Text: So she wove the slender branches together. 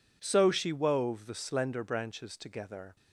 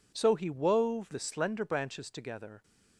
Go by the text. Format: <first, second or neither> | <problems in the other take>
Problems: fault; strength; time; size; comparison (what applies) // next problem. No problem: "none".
first | says "he" for "she"; at 0.3 s